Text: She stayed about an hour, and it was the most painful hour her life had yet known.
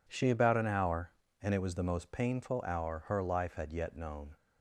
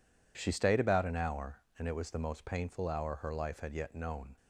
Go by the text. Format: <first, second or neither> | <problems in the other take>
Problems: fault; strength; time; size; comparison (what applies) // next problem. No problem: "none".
second | skips "stayed"; at 0.2 s